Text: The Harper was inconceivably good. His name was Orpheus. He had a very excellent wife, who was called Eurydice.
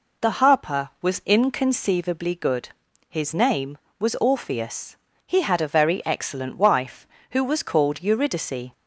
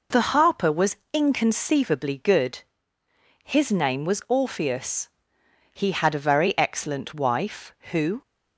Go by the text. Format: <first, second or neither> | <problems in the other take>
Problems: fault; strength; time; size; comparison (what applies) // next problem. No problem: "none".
first | pauses between "was" and "inconceivably"; slight; at 0.9 s; 0.16 s long // stops before "was called Eurydice"; at 8.2 s